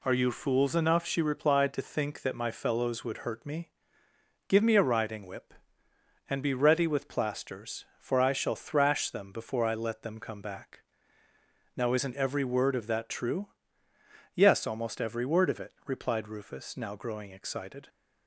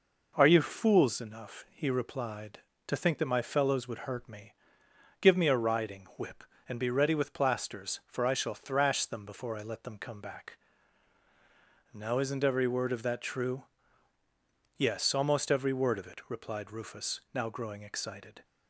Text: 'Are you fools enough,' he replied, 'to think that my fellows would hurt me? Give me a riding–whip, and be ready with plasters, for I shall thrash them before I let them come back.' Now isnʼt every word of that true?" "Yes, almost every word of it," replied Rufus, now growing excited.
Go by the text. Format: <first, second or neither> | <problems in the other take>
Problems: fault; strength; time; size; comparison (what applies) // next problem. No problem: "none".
second | says "she" for "he"; at 1.0 s